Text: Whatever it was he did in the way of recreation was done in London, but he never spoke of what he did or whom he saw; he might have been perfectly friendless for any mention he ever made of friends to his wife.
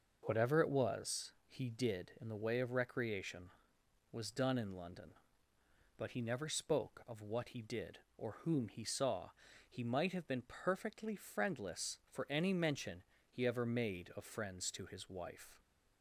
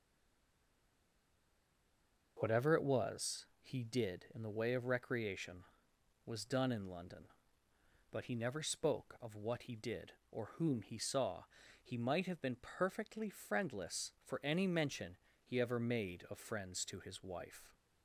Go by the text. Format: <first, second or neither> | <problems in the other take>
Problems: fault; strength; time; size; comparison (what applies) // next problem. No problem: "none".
first | stays silent before the first word; until 2.3 s; 2.3 s long // pauses between "mention" and "he"; slight; at 15.1 s; 0.26 s long; slight in the first